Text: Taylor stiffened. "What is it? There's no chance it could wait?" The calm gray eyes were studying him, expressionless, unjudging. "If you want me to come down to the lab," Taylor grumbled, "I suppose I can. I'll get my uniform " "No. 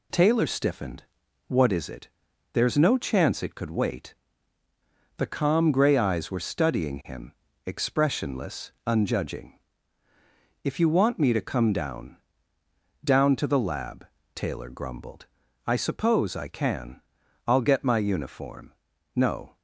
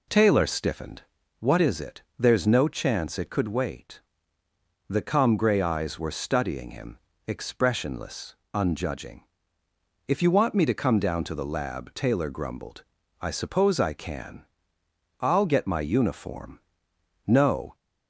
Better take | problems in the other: second | says "down" twice; at 13.0 s

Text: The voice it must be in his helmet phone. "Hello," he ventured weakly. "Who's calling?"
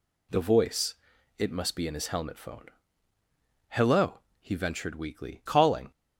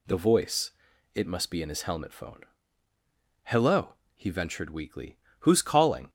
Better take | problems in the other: second | pauses between "voice" and "it"; at 0.9 s; 0.44 s long; also in the second // skips "Who's"; at 5.4 s

